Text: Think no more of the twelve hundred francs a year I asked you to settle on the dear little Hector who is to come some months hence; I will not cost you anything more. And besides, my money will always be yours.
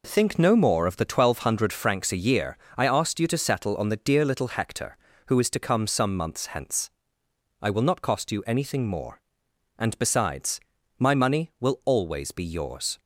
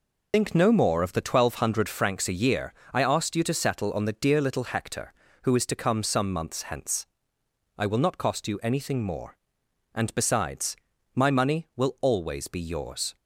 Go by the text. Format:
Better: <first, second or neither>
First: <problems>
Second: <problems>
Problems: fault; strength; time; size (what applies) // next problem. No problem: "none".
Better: first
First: pauses between "year" and "I"; slight; at 2.5 s; 0.20 s long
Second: loses the start of "Think"; at 0.3 s; 135 ms // pauses between "year" and "I"; slight; at 2.7 s; 0.20 s long